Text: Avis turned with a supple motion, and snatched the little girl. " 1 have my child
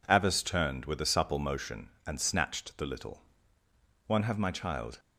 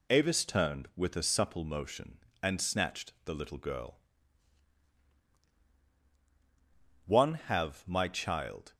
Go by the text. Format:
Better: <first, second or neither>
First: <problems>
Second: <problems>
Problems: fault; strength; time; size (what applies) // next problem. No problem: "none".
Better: second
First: skips "girl"; at 3.4 s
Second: none